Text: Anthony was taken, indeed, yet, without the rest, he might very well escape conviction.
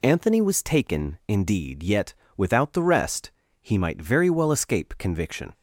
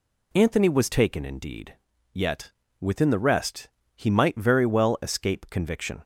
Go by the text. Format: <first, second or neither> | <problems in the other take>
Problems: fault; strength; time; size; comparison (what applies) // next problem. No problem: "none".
first | says "within" for "without"; at 2.7 s